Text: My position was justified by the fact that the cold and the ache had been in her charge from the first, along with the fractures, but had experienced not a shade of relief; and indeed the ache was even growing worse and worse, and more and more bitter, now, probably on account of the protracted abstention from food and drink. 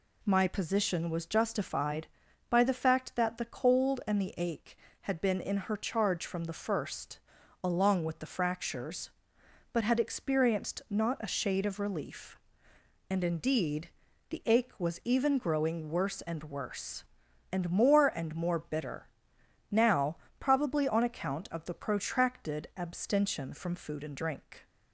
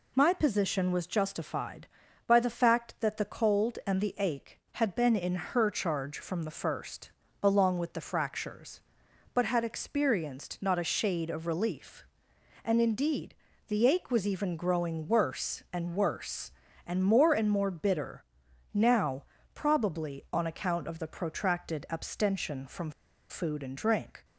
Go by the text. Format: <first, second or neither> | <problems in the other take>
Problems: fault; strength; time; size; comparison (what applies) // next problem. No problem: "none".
first | pauses between "indeed" and "the"; slight; at 13.3 s; 0.32 s long; also in the first // pauses between "from" and "food"; at 22.9 s; 0.38 s long